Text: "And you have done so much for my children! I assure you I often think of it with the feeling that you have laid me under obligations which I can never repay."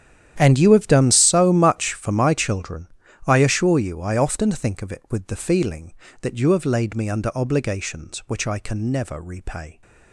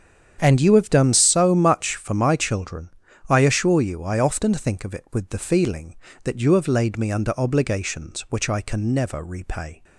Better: second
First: gets quieter; strong; throughout; 17 dB // starts louder than the rest; strong; until 1.4 s; 9.5 dB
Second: starts louder than the rest; strong; until 1.4 s; 7.5 dB

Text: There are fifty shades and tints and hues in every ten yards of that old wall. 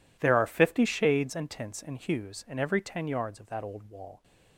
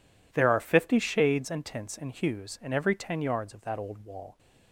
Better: second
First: gets quieter; strong; throughout; 17.5 dB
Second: none

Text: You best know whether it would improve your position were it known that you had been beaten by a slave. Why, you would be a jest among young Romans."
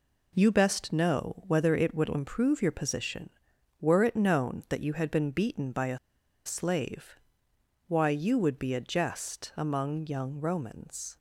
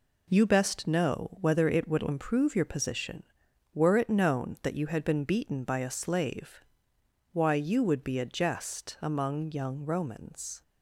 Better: second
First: pauses between "a" and "slave"; noticeable; at 5.9 s; 0.47 s long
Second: none

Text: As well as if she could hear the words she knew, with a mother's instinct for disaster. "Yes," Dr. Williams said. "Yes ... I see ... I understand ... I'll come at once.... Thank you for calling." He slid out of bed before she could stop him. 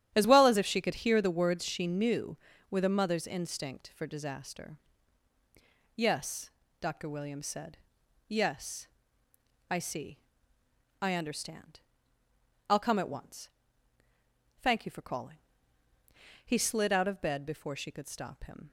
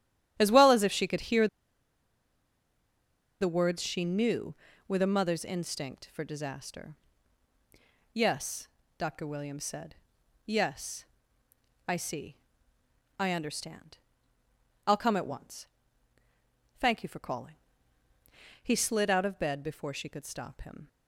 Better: first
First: starts louder than the rest; strong; until 1.1 s; 10 dB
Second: starts louder than the rest; strong; until 1.3 s; 10 dB // pauses between "hear" and "the"; strong; at 1.4 s; 1.9 s long

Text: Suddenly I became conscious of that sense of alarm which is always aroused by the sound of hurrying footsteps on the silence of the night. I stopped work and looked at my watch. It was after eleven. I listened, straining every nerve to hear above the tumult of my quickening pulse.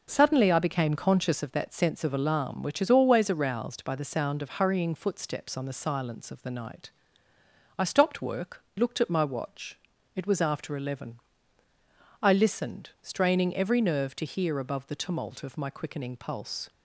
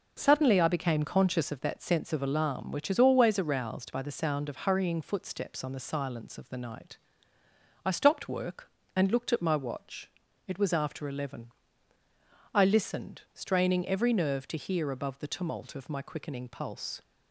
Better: second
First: skips "and"; at 8.7 s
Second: none

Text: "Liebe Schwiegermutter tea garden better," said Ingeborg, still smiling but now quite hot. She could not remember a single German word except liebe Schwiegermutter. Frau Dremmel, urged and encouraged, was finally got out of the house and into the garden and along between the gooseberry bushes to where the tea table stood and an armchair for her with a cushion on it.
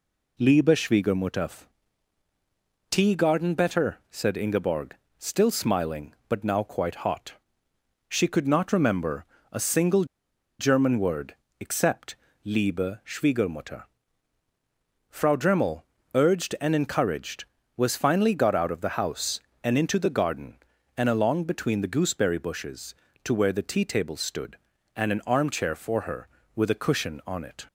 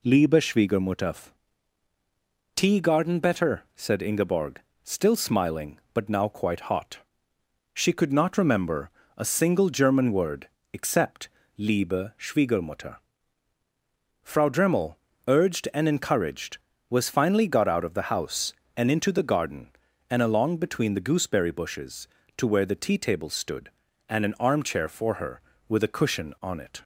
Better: second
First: pauses between "Schwiegermutter" and "tea"; strong; at 1.6 s; 1.2 s long // pauses between "remember" and "a"; slight; at 9.2 s; 0.26 s long // pauses between "single" and "German"; noticeable; at 10.0 s; 0.54 s long // pauses between "word" and "except"; slight; at 11.3 s; 0.24 s long // pauses between "except" and "liebe"; slight; at 12.1 s; 0.28 s long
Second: pauses between "Schwiegermutter" and "tea"; strong; at 1.2 s; 1.2 s long // pauses between "remember" and "a"; slight; at 8.8 s; 0.26 s long // pauses between "word" and "except"; slight; at 10.4 s; 0.24 s long // pauses between "except" and "liebe"; slight; at 11.2 s; 0.28 s long

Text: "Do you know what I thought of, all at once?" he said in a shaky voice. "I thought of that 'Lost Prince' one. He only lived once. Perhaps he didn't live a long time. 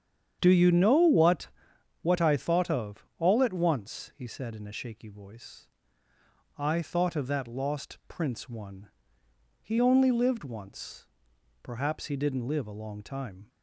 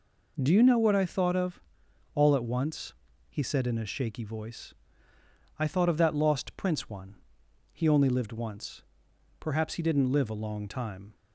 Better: second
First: starts louder than the rest; strong; until 1.4 s; 8.5 dB // says "what" twice; at 2.0 s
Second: none

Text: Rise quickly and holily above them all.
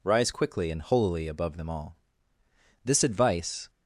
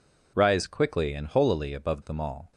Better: second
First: goes on to say "This advice"; noticeable; from 2.8 s on; 0.86 s long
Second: none

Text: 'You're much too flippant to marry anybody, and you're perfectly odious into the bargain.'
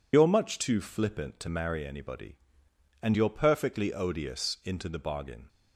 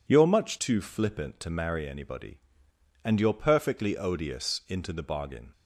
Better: second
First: loses the start of "You're"; at 0.1 s; 40 ms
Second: none

